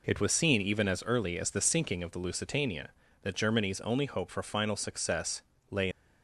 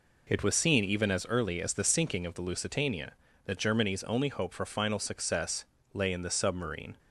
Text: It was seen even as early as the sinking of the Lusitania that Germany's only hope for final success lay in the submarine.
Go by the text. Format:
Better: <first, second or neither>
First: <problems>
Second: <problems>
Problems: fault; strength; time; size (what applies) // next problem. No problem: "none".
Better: second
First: pauses between "success" and "lay"; slight; at 5.4 s; 0.30 s long // stops before "in the submarine"; at 5.9 s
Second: pauses between "success" and "lay"; slight; at 5.6 s; 0.30 s long